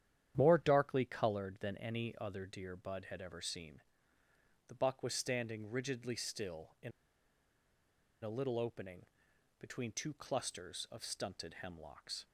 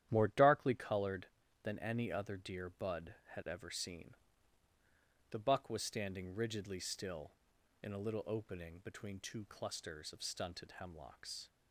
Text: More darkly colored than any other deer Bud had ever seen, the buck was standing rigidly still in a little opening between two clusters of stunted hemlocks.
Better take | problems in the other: second | starts louder than the rest; strong; until 1.3 s; 10 dB; strong in the second // pauses between "in" and "a"; strong; at 6.9 s; 1.3 s long // pauses between "opening" and "between"; noticeable; at 9.0 s; 0.52 s long

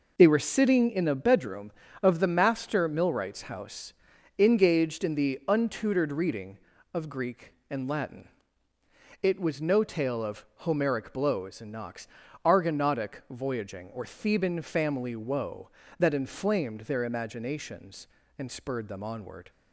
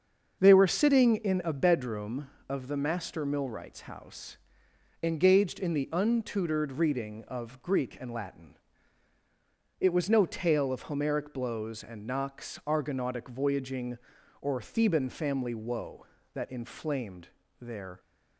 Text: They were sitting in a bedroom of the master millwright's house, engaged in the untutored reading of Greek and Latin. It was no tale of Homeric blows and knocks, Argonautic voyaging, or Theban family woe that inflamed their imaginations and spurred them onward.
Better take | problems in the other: first | starts louder than the rest; until 1.4 s; 6.5 dB // pauses between "inflamed" and "their"; slight; at 17.2 s; 0.32 s long // stops before "imaginations and spurred them onward"; at 17.9 s

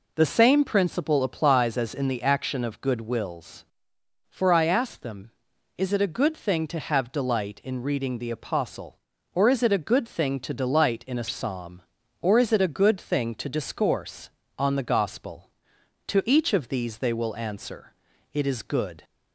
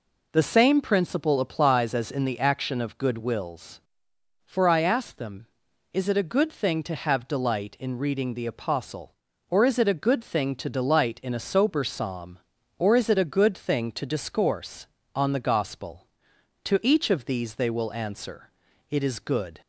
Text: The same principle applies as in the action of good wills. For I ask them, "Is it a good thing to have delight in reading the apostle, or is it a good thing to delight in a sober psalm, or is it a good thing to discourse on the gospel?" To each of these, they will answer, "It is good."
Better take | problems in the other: second | skips "sober"; at 11.2 s

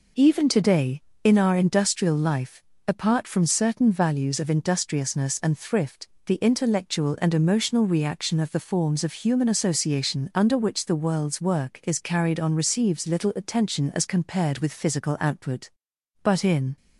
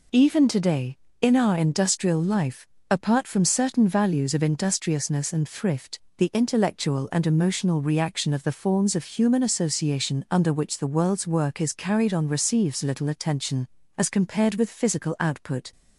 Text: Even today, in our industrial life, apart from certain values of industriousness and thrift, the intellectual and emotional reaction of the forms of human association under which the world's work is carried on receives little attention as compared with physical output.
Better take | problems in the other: second | goes on to say "But in"; from 16.2 s on; 0.54 s long

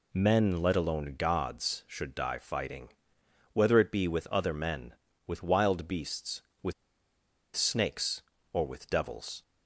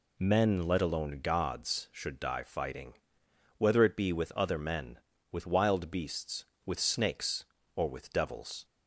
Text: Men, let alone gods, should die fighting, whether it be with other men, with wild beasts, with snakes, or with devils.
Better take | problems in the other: second | pauses between "with" and "snakes"; noticeable; at 6.7 s; 0.82 s long

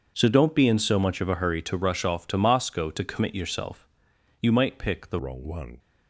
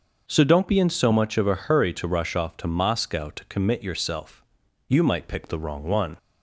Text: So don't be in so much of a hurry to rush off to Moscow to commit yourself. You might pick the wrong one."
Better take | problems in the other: second | starts louder than the rest; until 1.1 s; 6.5 dB; also in the second // changes voice at "wrong"; from 5.1 s on; 0.6 s long

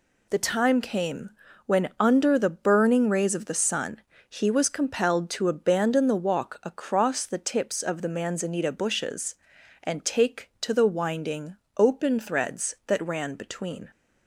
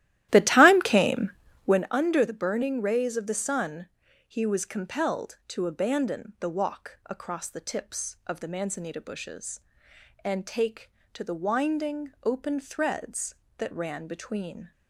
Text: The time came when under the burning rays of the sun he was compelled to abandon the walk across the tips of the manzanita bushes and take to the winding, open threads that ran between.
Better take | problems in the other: first | starts louder than the rest; strong; until 1.9 s; 14 dB // pauses between "came" and "when"; slight; at 1.3 s; 0.34 s long; slight in the first // pauses between "sun" and "he"; at 3.8 s; 0.38 s long; slight in the first

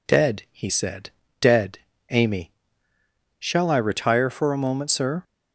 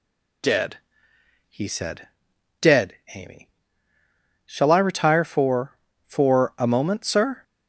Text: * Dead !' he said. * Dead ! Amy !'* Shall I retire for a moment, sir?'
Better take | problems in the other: first | says "for" twice; at 6.0 s

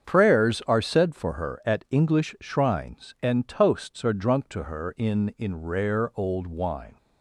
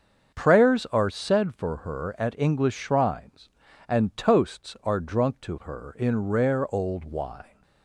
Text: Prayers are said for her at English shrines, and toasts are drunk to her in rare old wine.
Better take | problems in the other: second | starts louder than the rest; strong; until 1.1 s; 7.5 dB; also in the second // says "in" twice; at 5.3 s

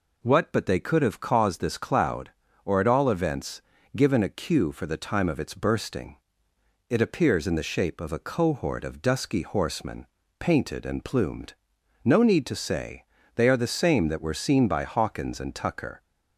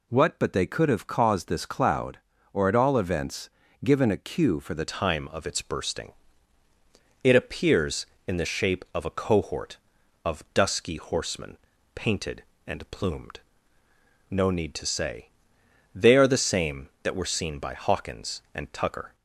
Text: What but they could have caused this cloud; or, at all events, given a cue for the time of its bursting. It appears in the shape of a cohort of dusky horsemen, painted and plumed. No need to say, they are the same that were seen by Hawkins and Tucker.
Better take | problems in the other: first | changes voice at "time"; from 4.9 s on; 14.2 s long

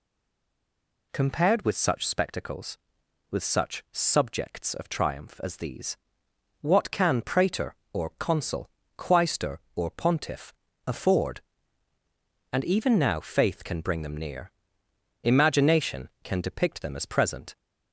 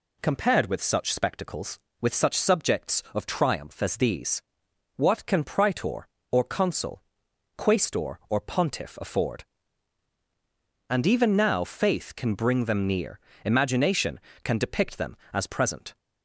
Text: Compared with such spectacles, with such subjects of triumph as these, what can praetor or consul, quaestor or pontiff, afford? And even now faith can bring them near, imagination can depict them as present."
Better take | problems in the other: second | stays silent before the first word; until 1.1 s; 1.1 s long

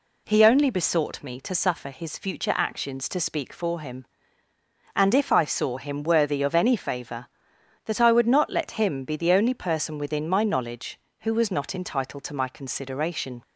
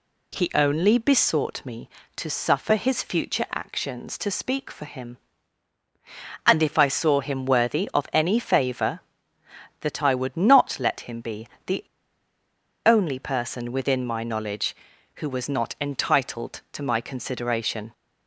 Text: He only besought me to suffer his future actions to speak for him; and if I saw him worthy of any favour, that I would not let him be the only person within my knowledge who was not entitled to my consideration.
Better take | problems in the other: first | pauses between "be" and "the"; slight; at 11.4 s; 0.20 s long // pauses between "the" and "only"; at 11.8 s; 1.0 s long

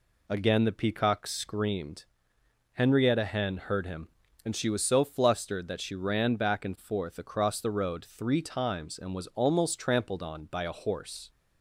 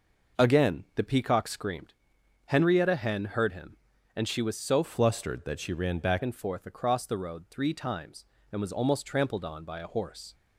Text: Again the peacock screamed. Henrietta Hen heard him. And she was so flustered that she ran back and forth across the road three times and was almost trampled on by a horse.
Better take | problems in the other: first | changes voice from "flustered" to "back"; from 4.8 to 6.2 s; 1.4 s long

